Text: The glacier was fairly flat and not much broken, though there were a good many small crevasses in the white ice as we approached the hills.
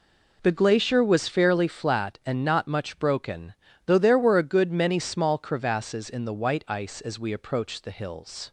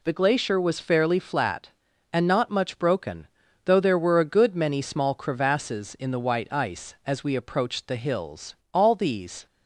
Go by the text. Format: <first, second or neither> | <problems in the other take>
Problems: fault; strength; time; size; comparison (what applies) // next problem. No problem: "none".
first | goes on to say "All these"; noticeable; from 8.7 s on; 0.72 s long